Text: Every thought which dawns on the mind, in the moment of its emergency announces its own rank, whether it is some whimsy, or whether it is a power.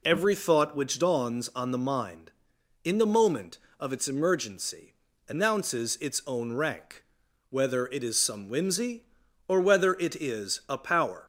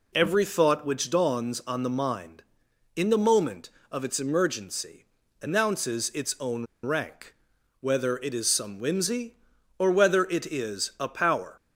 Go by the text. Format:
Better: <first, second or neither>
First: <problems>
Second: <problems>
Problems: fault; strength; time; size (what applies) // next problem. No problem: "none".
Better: first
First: pauses between "emergency" and "announces"; slight; at 4.9 s; 0.32 s long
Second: pauses between "emergency" and "announces"; slight; at 5.0 s; 0.34 s long // pauses between "own" and "rank"; slight; at 6.6 s; 0.17 s long